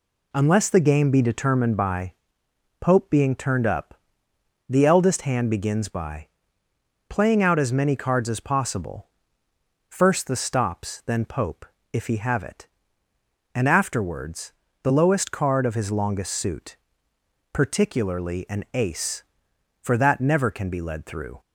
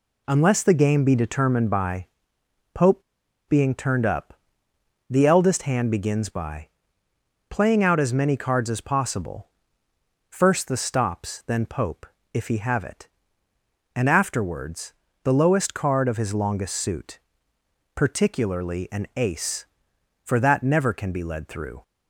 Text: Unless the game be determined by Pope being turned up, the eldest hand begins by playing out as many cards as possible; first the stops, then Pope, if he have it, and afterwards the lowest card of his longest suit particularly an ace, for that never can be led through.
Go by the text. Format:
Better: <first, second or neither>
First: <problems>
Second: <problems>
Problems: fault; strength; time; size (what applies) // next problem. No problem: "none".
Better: first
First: pauses between "by" and "Pope"; noticeable; at 2.1 s; 0.68 s long // pauses between "by" and "playing"; noticeable; at 6.2 s; 0.80 s long // pauses between "afterwards" and "the"; slight; at 14.5 s; 0.30 s long // pauses between "suit" and "particularly"; noticeable; at 16.7 s; 0.76 s long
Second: pauses between "by" and "Pope"; noticeable; at 2.0 s; 0.68 s long // pauses between "Pope" and "being"; noticeable; at 3.0 s; 0.46 s long // pauses between "by" and "playing"; noticeable; at 6.6 s; 0.80 s long // pauses between "afterwards" and "the"; slight; at 14.9 s; 0.30 s long // pauses between "suit" and "particularly"; noticeable; at 17.1 s; 0.76 s long